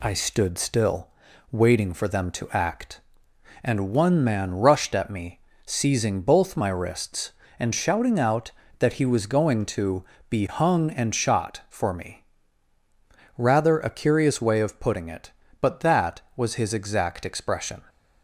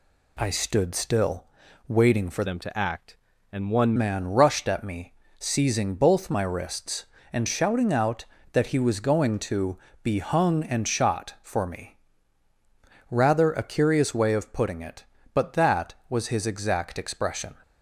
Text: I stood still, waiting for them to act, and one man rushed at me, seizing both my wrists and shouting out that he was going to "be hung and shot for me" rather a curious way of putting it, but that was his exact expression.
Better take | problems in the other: first | changes voice from "them" to "one"; from 2.4 to 3.9 s; 1.5 s long // pauses between "to" and "be"; slight; at 9.7 s; 0.28 s long; slight in the first // pauses between "me" and "rather"; at 11.9 s; 1.1 s long; also in the first

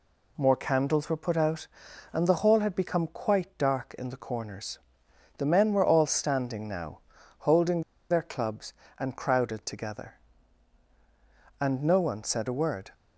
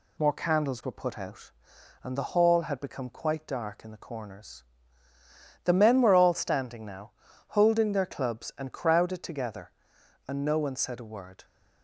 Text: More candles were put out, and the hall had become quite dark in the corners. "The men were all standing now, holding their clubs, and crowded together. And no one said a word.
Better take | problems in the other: second | pauses between "holding" and "their"; slight; at 7.8 s; 0.27 s long

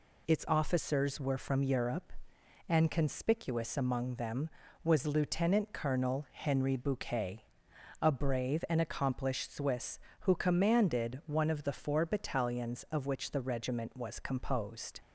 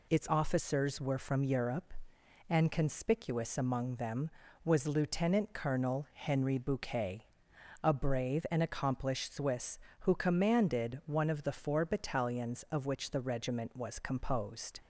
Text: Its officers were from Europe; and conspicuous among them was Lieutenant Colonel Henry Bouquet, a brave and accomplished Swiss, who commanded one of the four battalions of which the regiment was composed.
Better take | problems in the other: neither | none

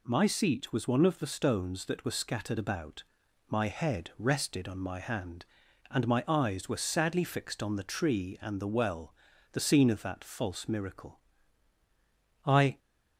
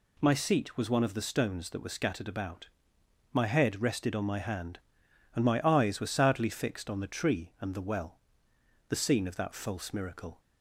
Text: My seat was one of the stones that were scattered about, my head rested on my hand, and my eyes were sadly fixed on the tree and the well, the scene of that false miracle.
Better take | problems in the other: second | goes on to say "I"; slight; from 12.4 s on; 0.34 s long

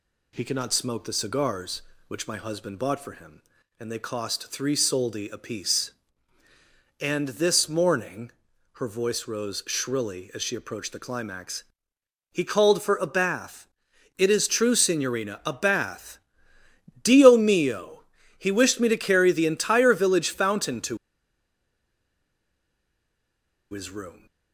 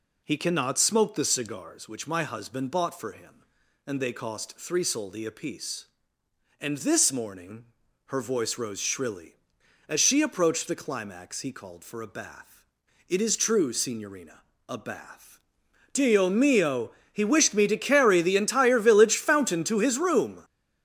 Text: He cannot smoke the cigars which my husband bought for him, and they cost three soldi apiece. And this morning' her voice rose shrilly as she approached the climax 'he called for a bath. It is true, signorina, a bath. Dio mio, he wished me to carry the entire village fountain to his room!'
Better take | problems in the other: second | pauses between "morning" and "her"; noticeable; at 8.3 s; 0.46 s long; also in the second // pauses between "climax" and "he"; noticeable; at 11.6 s; 0.70 s long // pauses between "to" and "his"; strong; at 20.9 s; 2.7 s long

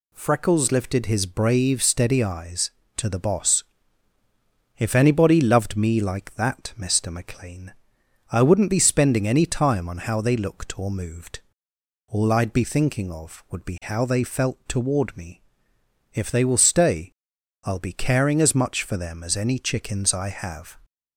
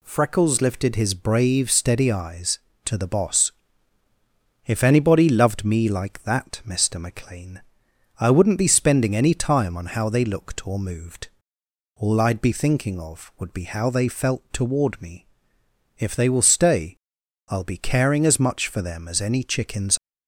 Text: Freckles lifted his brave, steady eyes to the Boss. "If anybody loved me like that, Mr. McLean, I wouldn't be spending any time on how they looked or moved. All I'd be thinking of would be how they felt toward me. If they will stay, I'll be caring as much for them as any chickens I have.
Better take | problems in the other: first | stops before "I have"; at 19.9 s

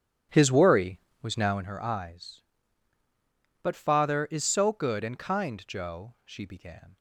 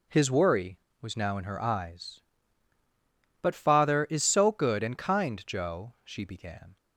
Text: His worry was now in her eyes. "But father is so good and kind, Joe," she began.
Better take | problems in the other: second | starts louder than the rest; strong; until 1.7 s; 11 dB

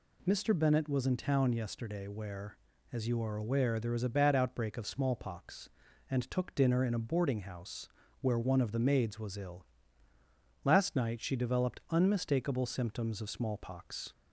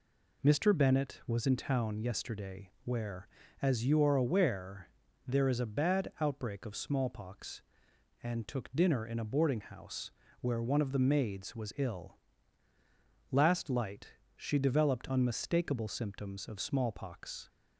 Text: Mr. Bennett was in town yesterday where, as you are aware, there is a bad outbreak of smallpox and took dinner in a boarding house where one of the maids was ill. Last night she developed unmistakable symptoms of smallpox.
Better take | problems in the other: first | pauses between "house" and "where"; slight; at 10.1 s; 0.28 s long; slight in the first // says "light" for "night"; at 13.6 s

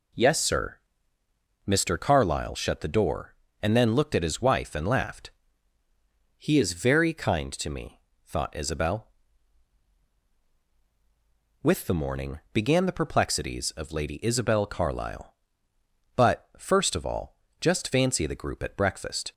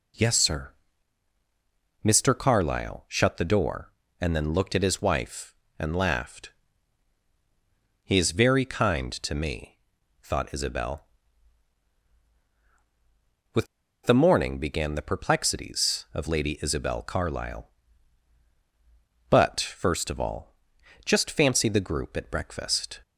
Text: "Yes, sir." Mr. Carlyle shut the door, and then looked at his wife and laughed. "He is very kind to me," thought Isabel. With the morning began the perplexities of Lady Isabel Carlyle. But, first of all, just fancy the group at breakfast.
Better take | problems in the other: first | pauses between "With" and "the"; at 13.6 s; 0.38 s long

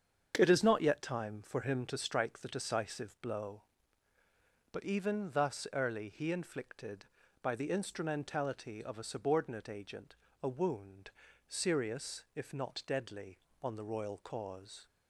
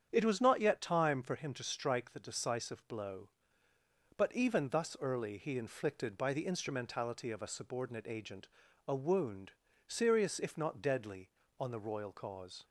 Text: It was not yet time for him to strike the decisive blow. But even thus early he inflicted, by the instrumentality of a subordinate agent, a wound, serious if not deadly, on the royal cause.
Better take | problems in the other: second | starts louder than the rest; strong; until 1.4 s; 7.5 dB; strong in the second // says "is" for "was"; at 0.4 s

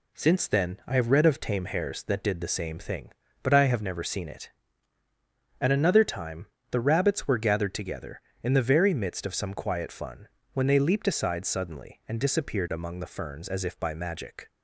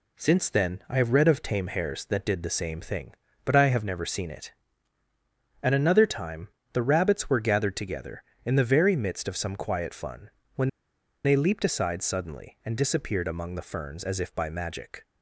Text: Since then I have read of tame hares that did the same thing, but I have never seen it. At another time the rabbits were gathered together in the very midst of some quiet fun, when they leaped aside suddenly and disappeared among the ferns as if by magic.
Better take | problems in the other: first | pauses between "time" and "the"; slight; at 6.4 s; 0.26 s long; slight in the first // pauses between "when" and "they"; noticeable; at 10.6 s; 0.56 s long

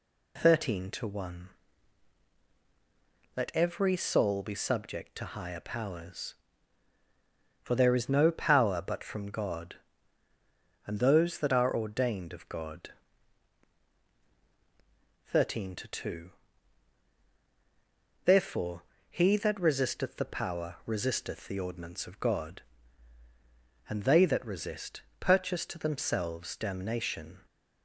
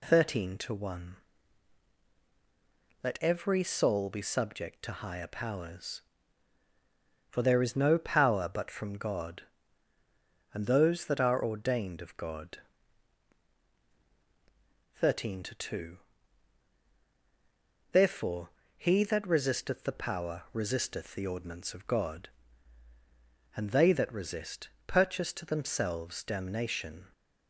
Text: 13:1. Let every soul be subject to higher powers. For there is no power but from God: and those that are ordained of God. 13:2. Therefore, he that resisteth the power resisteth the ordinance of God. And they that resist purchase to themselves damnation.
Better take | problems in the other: neither | pauses between "resist" and "purchase"; slight; the same in both

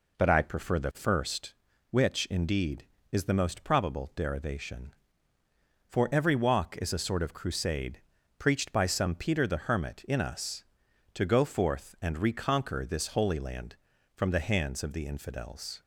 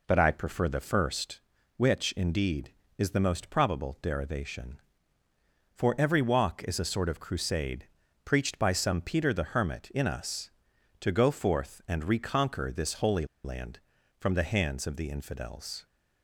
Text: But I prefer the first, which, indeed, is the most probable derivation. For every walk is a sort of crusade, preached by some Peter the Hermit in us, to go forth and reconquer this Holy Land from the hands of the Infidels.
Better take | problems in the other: first | pauses between "Holy" and "Land"; slight; at 13.2 s; 0.18 s long

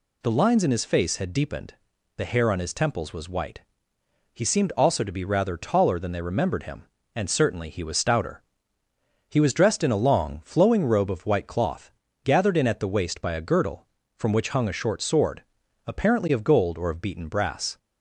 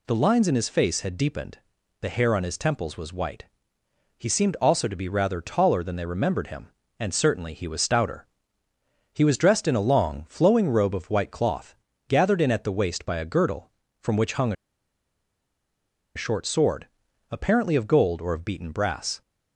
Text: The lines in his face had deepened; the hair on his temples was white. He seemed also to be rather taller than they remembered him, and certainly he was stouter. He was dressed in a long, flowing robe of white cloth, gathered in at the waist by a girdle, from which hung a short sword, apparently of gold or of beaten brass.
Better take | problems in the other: first | pauses between "hung" and "a"; strong; at 14.5 s; 1.6 s long

